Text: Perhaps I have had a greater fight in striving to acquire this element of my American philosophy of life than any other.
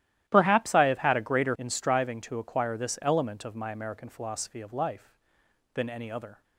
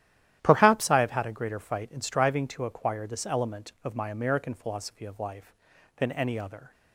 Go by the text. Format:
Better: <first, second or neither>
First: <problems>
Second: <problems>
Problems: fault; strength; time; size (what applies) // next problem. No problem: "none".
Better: second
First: starts louder than the rest; strong; until 1.2 s; 13.5 dB // skips "fight"; at 1.5 s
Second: starts louder than the rest; strong; until 1.4 s; 12.5 dB